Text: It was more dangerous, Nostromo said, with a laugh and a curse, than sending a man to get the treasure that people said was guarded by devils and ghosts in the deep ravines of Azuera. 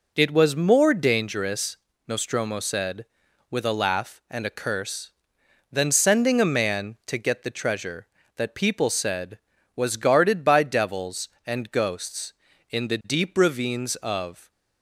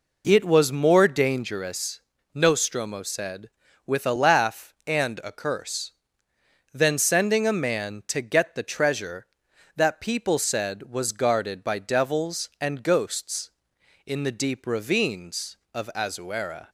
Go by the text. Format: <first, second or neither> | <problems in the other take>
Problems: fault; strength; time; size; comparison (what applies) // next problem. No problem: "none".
second | stops before "Azuera"; at 14.4 s